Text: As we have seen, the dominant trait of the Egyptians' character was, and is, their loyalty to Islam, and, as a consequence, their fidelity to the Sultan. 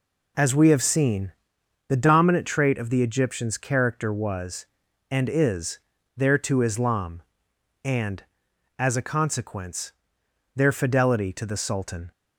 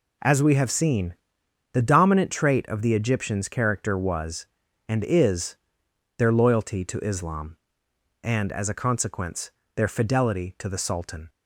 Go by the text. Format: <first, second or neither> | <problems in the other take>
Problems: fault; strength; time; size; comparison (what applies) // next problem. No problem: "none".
second | skips "loyalty"; at 6.3 s